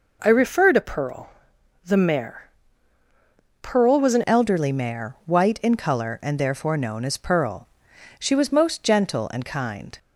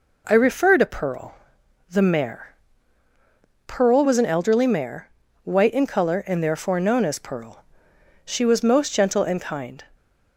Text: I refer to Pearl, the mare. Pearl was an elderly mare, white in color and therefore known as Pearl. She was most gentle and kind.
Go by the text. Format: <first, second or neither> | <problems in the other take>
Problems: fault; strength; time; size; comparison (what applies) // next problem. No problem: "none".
second | changes voice at "elderly"; from 4.2 s on; 5.7 s long